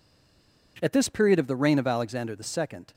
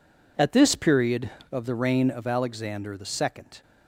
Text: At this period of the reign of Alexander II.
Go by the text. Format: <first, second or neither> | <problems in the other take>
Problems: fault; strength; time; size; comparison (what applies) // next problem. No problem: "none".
second | stays silent before the first word; slight; until 0.7 s; 0.7 s long